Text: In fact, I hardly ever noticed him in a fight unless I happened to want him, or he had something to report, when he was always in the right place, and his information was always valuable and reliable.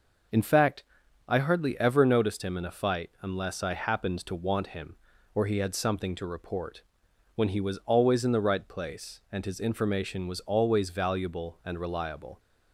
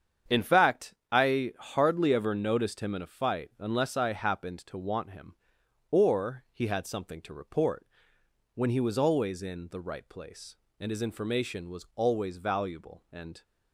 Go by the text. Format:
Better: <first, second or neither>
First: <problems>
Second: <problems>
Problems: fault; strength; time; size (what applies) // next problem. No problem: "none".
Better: first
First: none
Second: starts louder than the rest; strong; until 1.4 s; 8 dB // stops before "reliable"; at 13.4 s